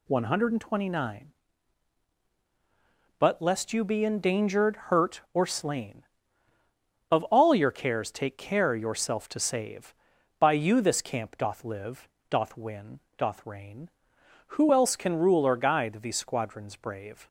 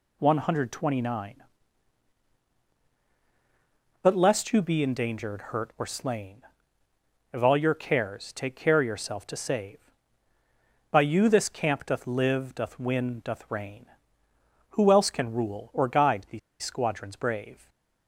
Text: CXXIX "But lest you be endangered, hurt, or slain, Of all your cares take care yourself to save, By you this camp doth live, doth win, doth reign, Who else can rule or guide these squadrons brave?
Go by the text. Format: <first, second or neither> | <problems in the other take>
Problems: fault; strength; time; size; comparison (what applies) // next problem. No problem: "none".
first | pauses between "these" and "squadrons"; slight; at 16.3 s; 0.23 s long